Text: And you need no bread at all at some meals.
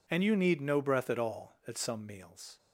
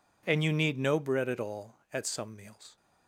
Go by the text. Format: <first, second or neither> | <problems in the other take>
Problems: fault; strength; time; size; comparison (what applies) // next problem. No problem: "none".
second | says "breath" for "bread"; at 0.8 s